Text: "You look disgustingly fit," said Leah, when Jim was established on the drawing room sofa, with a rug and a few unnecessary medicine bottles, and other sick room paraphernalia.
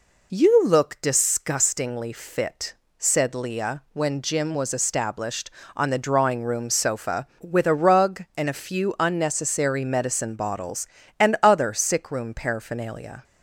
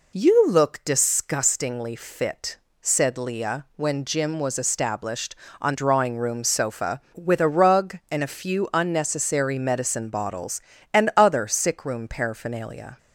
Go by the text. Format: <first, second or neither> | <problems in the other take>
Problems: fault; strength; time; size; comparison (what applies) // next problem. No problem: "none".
first | skips "the"; at 5.7 s